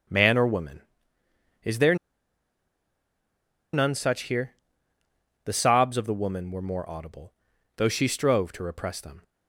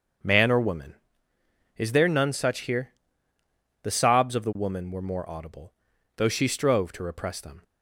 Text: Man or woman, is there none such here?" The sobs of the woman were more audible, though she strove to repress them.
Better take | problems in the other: second | starts louder than the rest; until 1.9 s; 7 dB; also in the second // pauses between "there" and "none"; strong; at 1.9 s; 1.7 s long

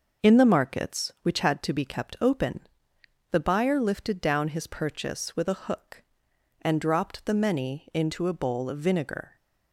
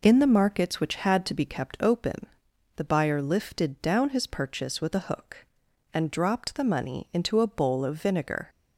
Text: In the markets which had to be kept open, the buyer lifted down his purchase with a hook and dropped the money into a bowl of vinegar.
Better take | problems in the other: second | starts louder than the rest; noticeable; until 1.3 s; 6 dB // says "many" for "money"; at 7.3 s

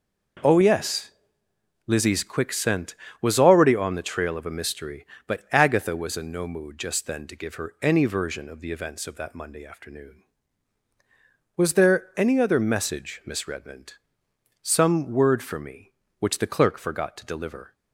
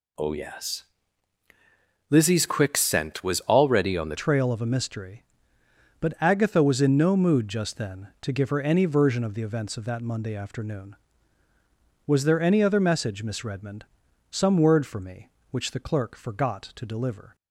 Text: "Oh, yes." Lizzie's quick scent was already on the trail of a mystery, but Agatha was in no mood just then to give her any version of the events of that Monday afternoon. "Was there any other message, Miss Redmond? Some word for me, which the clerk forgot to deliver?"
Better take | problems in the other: first | changes voice at "trail"; from 4.1 s on; 13.2 s long

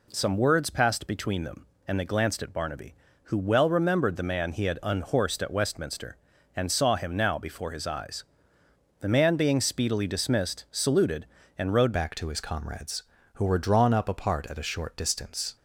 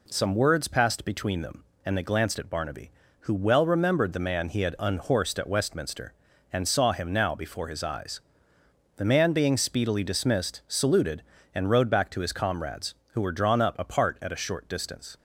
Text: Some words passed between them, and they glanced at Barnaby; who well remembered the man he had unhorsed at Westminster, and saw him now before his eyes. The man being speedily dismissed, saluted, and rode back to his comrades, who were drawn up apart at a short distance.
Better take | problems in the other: second | changes voice at "back"; from 11.9 s on; 3.6 s long

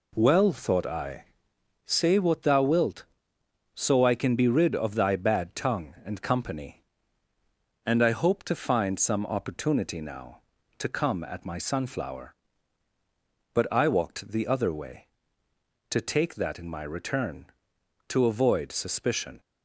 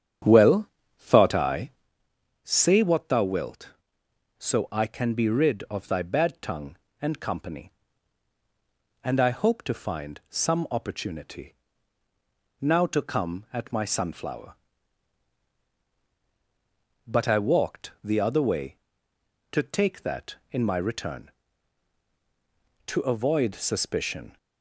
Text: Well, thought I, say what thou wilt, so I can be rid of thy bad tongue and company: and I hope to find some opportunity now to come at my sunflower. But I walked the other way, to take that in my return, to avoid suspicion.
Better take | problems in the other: first | starts louder than the rest; strong; until 1.9 s; 9.5 dB // pauses between "opportunity" and "now"; at 11.5 s; 1.0 s long

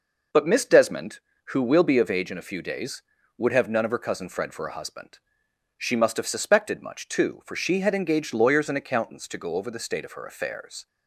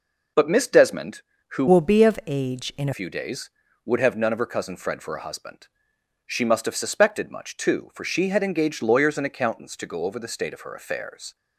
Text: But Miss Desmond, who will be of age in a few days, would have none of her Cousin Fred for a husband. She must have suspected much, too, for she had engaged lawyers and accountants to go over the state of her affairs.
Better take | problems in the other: first | changes voice from "will" to "a"; from 1.6 to 2.9 s; 1.3 s long

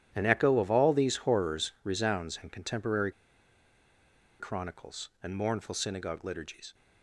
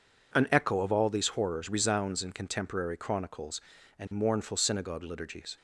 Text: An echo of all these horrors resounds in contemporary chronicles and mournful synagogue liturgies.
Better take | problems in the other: second | pauses between "contemporary" and "chronicles"; strong; at 3.1 s; 1.2 s long

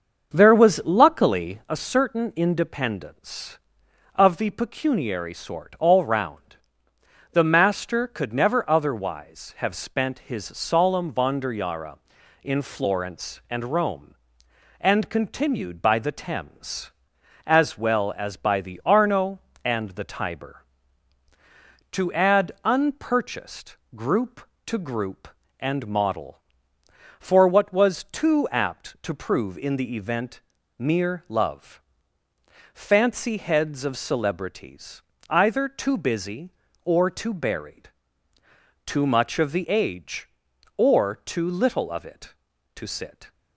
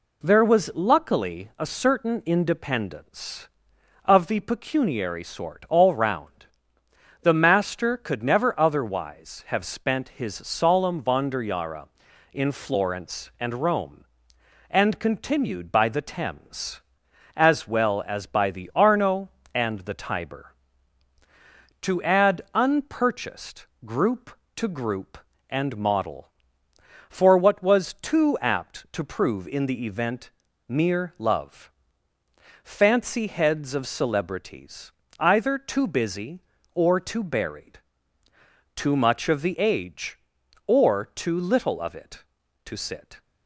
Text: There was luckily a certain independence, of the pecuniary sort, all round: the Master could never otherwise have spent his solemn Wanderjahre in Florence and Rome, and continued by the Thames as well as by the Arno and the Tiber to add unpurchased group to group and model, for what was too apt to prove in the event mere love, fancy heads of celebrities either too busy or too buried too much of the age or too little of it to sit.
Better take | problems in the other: second | starts louder than the rest; until 1.9 s; 6.5 dB // pauses between "unpurchased" and "group"; slight; at 23.7 s; 0.22 s long; slight in the second // pauses between "event" and "mere"; at 30.3 s; 0.40 s long; also in the second // pauses between "celebrities" and "either"; slight; at 35.0 s; 0.28 s long; slight in the second // pauses between "buried" and "too"; noticeable; at 37.8 s; 0.96 s long; noticeable in the second

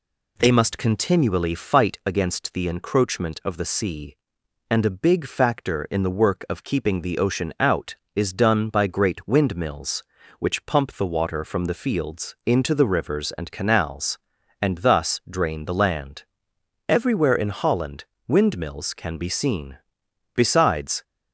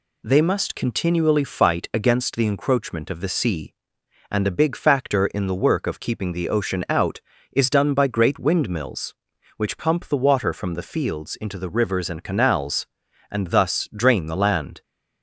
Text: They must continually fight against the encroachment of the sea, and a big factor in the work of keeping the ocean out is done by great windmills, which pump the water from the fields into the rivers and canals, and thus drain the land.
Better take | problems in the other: second | goes on to say "Everywhere in Holland windmills can be seen Besides"; strong; from 16.8 s on; 4.1 s long

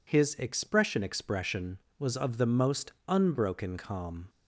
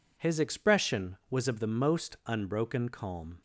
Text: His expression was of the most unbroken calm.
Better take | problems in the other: second | says "expression" twice; at 1.0 s // pauses between "most" and "unbroken"; slight; at 2.9 s; 0.16 s long

